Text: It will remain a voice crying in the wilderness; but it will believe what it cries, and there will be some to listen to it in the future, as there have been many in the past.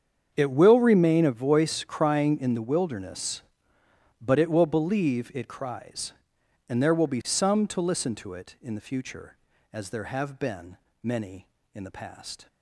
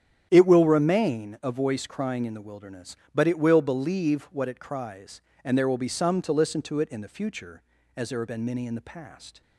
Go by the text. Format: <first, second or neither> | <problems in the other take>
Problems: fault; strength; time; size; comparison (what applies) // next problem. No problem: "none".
second | starts louder than the rest; strong; until 1.3 s; 7.5 dB; strong in the second // skips "what"; at 5.3 s // pauses between "been" and "many"; slight; at 10.7 s; 0.26 s long